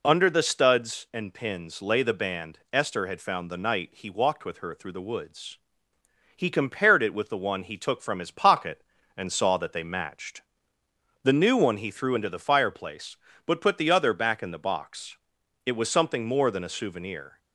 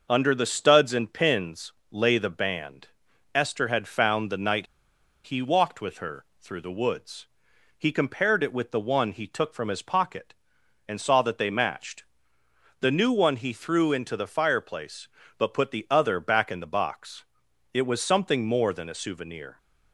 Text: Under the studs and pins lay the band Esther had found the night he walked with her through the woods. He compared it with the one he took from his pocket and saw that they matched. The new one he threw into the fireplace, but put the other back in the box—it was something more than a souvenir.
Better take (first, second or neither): first